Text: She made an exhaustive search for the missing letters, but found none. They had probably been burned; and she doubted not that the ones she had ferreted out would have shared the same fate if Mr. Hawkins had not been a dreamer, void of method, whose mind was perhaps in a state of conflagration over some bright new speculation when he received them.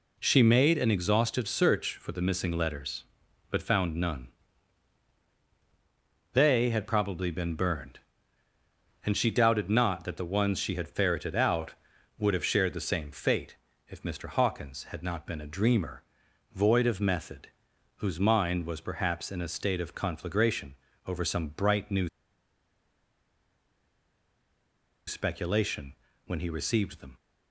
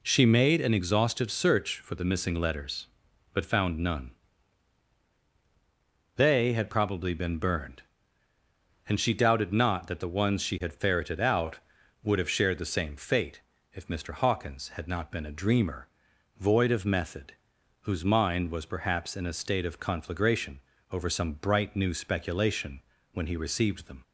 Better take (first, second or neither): second